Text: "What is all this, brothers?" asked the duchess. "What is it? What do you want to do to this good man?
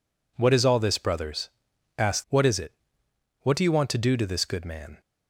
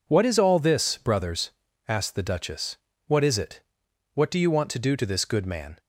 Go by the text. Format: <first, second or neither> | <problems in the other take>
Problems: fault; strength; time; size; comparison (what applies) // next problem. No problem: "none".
second | skips "the duchess"; at 2.2 s